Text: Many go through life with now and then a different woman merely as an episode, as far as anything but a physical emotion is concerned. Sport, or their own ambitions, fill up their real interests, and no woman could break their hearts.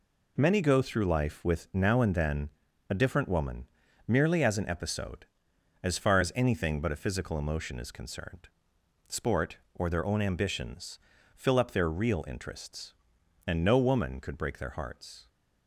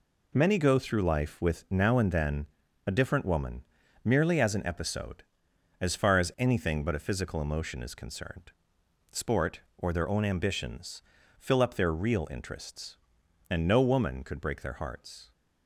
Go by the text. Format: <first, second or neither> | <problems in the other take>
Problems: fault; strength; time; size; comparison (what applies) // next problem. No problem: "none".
neither | pauses between "then" and "a"; the same in both // pauses between "woman" and "merely"; the same in both